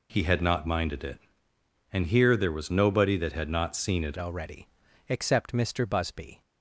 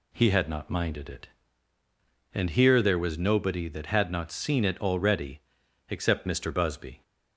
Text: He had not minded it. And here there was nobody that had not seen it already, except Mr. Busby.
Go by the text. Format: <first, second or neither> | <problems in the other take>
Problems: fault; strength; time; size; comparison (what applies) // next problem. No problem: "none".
second | changes voice at "already"; from 4.1 s on; 2.3 s long